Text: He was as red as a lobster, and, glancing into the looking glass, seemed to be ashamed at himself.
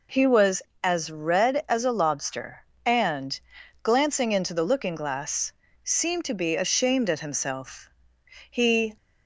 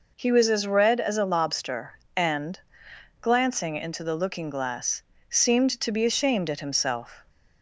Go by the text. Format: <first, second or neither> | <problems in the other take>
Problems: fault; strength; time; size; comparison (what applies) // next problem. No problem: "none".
second | goes on to say "He"; slight; from 8.4 s on; 0.46 s long